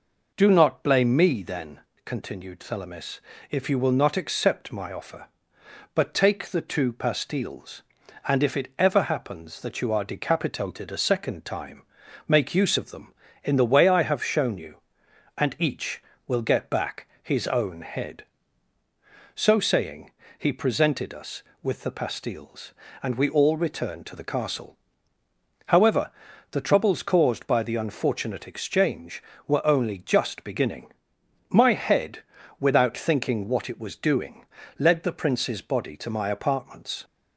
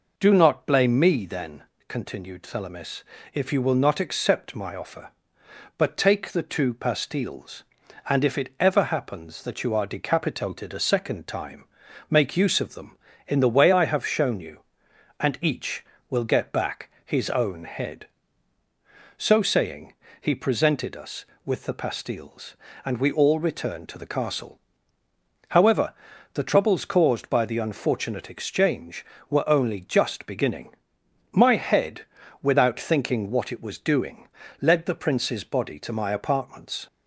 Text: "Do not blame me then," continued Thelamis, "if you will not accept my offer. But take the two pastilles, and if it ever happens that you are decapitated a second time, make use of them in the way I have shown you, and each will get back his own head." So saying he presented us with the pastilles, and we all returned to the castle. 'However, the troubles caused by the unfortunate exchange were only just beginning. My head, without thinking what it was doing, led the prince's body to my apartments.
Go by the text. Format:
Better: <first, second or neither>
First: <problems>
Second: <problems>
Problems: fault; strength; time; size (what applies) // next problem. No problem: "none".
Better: neither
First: pauses between "back" and "his"; slight; at 17.0 s; 0.16 s long // pauses between "saying" and "he"; slight; at 20.1 s; 0.26 s long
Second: pauses between "back" and "his"; slight; at 16.9 s; 0.16 s long // pauses between "saying" and "he"; slight; at 19.9 s; 0.26 s long